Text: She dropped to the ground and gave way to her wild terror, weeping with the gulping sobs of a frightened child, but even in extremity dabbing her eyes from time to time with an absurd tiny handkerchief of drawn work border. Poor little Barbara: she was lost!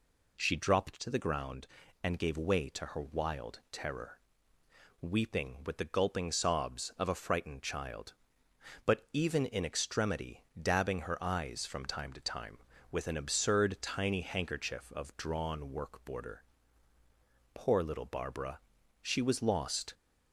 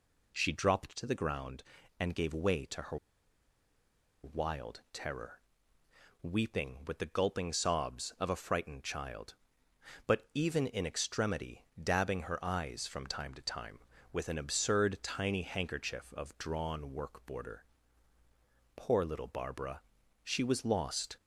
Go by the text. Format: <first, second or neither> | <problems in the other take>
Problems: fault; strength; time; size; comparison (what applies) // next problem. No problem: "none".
first | pauses between "her" and "wild"; strong; at 2.9 s; 1.2 s long // pauses between "extremity" and "dabbing"; slight; at 11.6 s; 0.18 s long; slight in the first